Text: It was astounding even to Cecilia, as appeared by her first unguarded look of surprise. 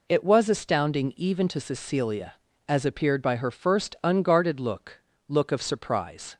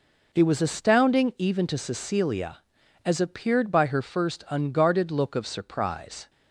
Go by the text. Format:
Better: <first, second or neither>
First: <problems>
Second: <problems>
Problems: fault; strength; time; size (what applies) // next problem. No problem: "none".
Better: second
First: says "look" twice; at 5.2 s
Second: none